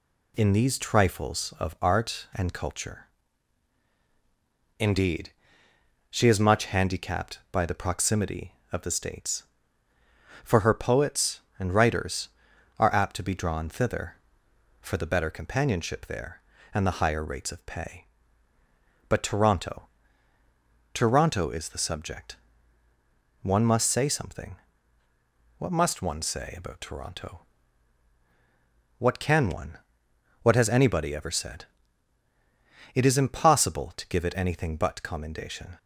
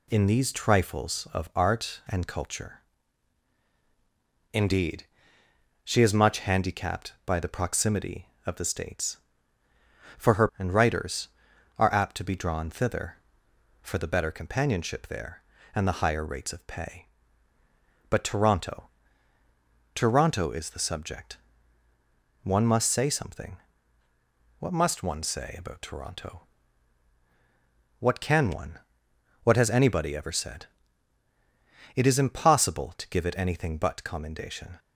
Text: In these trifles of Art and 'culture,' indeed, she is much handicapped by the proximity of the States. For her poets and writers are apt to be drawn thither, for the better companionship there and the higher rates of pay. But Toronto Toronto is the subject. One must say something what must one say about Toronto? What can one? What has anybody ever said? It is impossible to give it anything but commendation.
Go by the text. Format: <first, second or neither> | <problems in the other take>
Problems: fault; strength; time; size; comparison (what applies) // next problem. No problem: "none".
first | skips "poets"; at 10.5 s // pauses between "Toronto" and "Toronto"; at 18.8 s; 1.1 s long; also in the first // pauses between "something" and "what"; at 23.5 s; 1.0 s long; also in the first